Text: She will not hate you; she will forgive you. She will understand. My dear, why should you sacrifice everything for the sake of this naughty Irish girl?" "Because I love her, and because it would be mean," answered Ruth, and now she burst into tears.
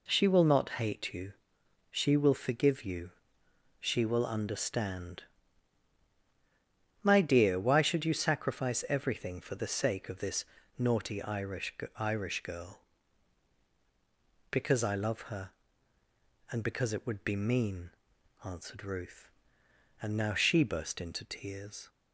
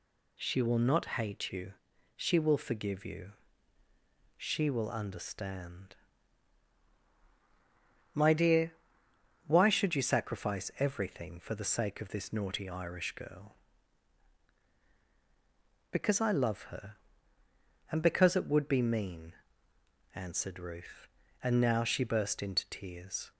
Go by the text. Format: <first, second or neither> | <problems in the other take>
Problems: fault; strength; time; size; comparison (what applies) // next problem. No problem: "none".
second | pauses between "this" and "naughty"; slight; at 10.4 s; 0.34 s long // says "Irish" twice; at 11.9 s